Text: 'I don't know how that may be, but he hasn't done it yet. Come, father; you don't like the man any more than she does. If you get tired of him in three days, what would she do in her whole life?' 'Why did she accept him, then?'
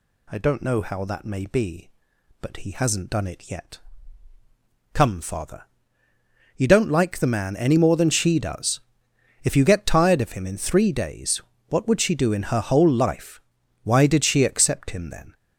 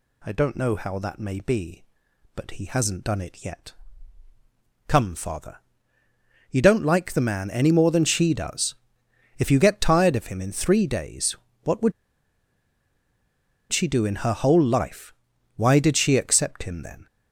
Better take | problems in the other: first | pauses between "would" and "she"; strong; at 11.9 s; 1.7 s long

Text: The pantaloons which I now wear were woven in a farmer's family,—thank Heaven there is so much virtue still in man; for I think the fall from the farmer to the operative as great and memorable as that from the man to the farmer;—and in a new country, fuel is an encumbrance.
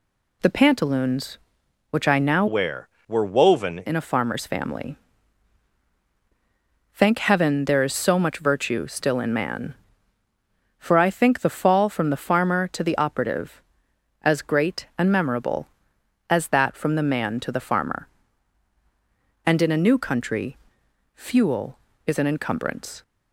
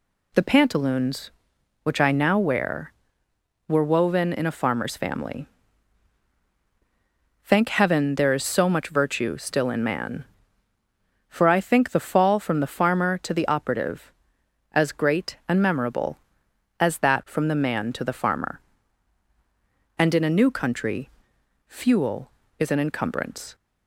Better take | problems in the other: second | changes voice from "wear" to "woven"; from 2.4 to 3.7 s; 1.3 s long

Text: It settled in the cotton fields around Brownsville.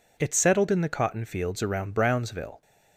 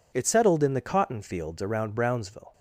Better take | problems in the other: neither | none

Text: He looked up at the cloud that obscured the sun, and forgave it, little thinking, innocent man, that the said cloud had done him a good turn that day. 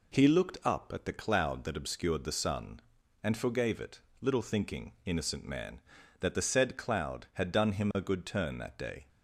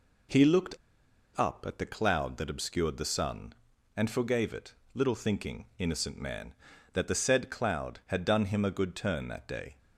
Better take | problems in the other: first | pauses between "looked" and "up"; noticeable; at 0.7 s; 0.59 s long

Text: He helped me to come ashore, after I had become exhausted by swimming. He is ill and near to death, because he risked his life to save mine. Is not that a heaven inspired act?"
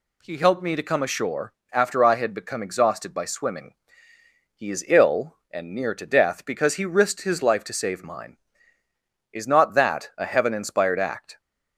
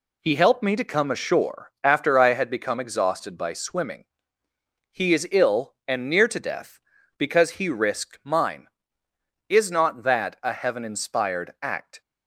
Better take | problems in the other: first | skips "his life to save"; at 8.2 s

